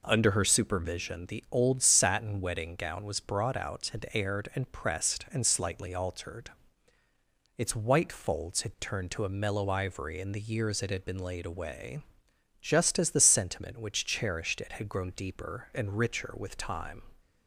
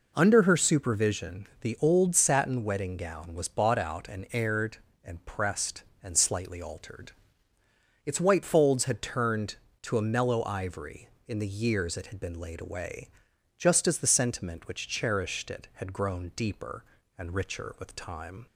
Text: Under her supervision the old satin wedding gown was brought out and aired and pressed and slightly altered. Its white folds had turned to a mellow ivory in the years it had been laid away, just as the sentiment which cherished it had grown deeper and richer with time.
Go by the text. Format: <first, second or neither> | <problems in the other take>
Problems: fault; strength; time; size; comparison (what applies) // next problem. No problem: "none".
first | pauses between "supervision" and "the"; slight; at 1.4 s; 0.16 s long // says "bought" for "brought"; at 3.4 s